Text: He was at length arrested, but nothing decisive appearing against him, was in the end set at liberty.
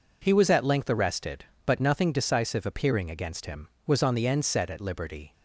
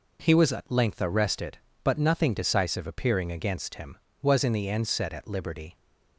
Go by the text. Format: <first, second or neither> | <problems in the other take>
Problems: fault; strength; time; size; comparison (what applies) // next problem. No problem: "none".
second | says "on" for "in"; at 4.0 s